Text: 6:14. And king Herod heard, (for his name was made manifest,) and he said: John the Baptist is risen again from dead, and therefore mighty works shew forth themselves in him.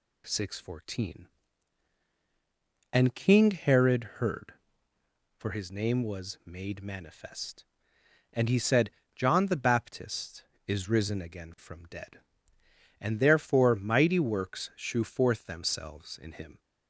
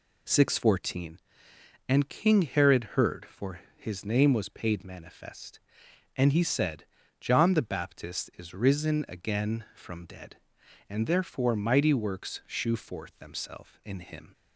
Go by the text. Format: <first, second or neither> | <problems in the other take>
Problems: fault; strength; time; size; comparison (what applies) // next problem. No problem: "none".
first | pauses between "for" and "his"; slight; at 3.6 s; 0.18 s long // says "paid" for "made"; at 4.4 s